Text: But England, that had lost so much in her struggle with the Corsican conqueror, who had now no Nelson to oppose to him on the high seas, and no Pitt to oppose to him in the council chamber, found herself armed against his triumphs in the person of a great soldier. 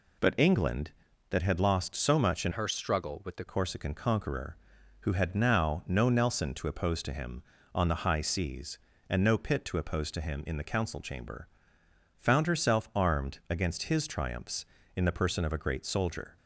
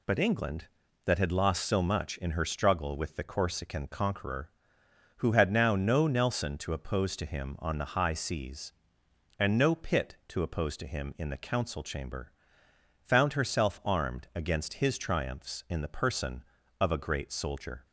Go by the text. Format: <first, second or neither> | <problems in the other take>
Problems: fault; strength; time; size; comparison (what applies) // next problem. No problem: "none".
second | changes voice from "her" to "the"; from 2.5 to 3.4 s; 0.9 s long